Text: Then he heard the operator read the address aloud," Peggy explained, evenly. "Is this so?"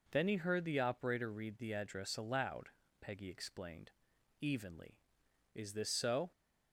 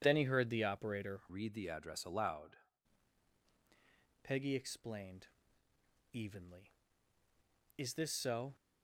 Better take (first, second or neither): first